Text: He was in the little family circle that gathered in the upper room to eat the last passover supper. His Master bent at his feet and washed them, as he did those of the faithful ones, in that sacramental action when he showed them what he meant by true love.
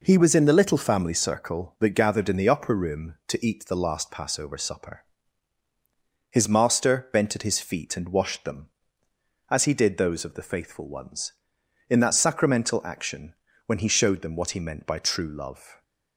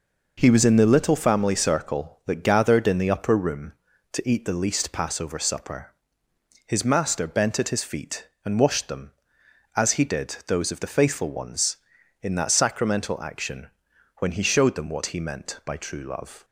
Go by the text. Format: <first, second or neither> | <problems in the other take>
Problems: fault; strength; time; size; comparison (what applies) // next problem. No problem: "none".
first | says "least" for "last"; at 4.6 s // pauses between "action" and "when"; noticeable; at 13.6 s; 0.52 s long; slight in the first